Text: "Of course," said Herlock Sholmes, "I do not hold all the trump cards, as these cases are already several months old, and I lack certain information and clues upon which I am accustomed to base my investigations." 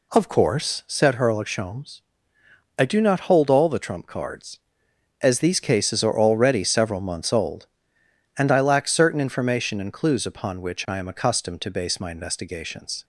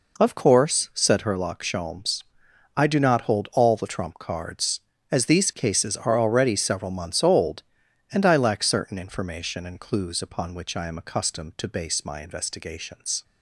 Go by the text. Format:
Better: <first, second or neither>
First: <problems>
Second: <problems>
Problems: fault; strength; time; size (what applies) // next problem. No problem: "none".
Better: neither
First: none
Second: none